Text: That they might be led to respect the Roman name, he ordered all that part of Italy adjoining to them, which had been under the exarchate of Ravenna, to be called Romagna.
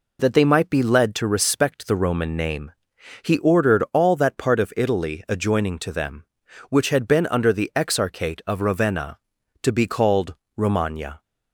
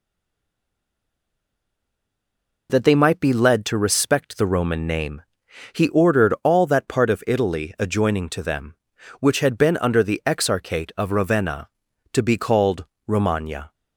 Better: first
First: pauses between "called" and "Romagna"; slight; at 10.3 s; 0.24 s long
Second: stays silent before the first word; strong; until 2.6 s; 2.6 s long // pauses between "called" and "Romagna"; slight; at 12.8 s; 0.24 s long

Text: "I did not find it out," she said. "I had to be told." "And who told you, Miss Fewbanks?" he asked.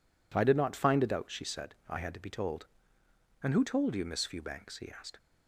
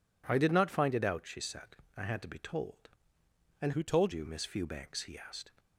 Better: first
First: none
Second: changes voice from "who" to "told"; from 3.7 to 4.1 s; 0.4 s long

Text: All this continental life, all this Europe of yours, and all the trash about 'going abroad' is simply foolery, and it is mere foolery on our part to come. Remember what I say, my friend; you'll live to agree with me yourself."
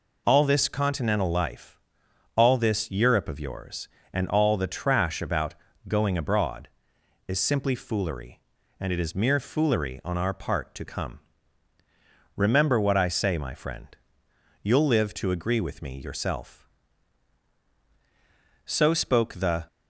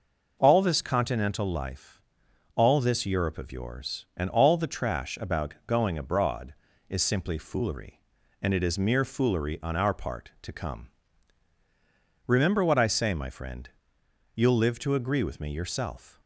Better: second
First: pauses between "about" and "going"; slight; at 5.5 s; 0.34 s long // goes on to say "So spoke the"; noticeable; from 18.6 s on; 1.0 s long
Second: none

